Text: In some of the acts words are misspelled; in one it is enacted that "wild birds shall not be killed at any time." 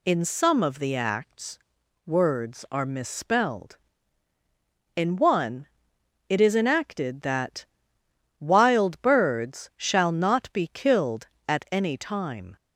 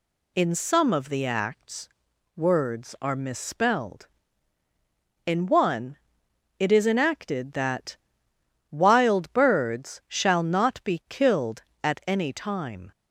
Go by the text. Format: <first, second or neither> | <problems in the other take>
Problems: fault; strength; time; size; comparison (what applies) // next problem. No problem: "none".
neither | pauses between "acts" and "words"; noticeable; the same in both // pauses between "one" and "it"; noticeable; the same in both // pauses between "that" and "wild"; noticeable; the same in both